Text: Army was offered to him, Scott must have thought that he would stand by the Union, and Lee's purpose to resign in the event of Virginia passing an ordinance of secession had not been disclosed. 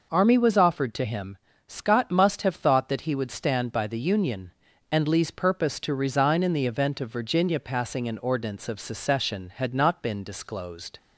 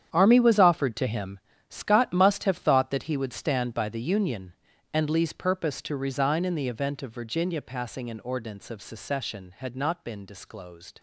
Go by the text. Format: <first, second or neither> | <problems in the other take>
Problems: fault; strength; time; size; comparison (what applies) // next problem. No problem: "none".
first | gets quieter; strong; throughout; 13.5 dB